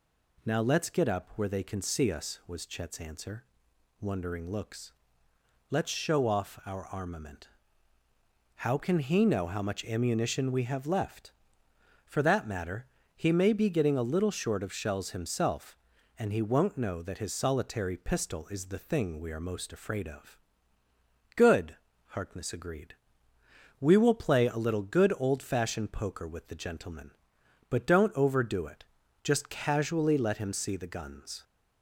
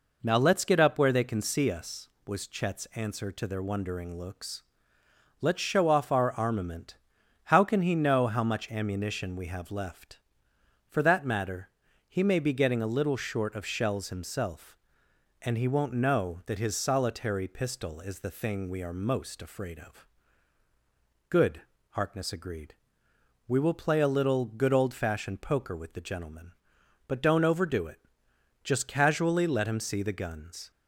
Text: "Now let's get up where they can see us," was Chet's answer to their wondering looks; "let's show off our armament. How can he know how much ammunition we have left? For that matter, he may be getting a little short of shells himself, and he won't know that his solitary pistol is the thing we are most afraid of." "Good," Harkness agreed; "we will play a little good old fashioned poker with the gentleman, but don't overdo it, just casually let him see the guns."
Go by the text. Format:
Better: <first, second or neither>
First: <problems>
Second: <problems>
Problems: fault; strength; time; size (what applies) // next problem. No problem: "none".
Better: second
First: skips "to their"; at 3.7 s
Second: none